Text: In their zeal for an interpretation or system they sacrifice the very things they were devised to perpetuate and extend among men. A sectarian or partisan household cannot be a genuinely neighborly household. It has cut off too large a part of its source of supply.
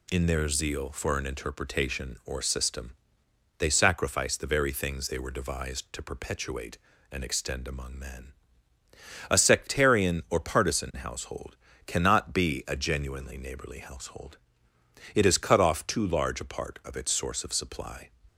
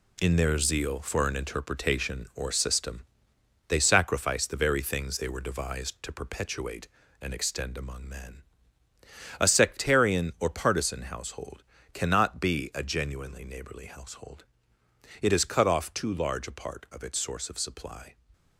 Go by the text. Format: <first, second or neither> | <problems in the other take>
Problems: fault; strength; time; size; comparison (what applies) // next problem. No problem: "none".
first | gets quieter; strong; throughout; 7.5 dB // pauses between "system" and "they"; noticeable; at 3.0 s; 0.64 s long; noticeable in the first // pauses between "household" and "cannot"; slight; at 11.6 s; 0.30 s long; slight in the first